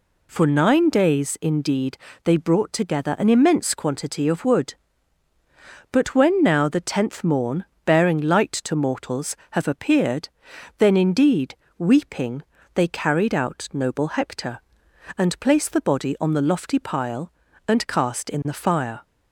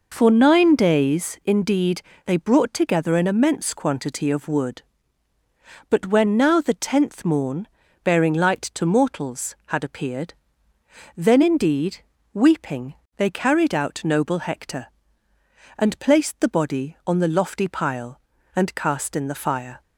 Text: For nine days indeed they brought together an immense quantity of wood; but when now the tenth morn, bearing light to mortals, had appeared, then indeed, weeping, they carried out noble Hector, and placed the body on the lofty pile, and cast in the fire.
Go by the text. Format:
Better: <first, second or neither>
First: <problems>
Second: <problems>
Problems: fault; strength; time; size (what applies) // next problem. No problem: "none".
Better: second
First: pauses between "indeed" and "they"; slight; at 1.9 s; 0.24 s long // says "have" for "had"; at 9.4 s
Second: pauses between "indeed" and "they"; slight; at 2.0 s; 0.24 s long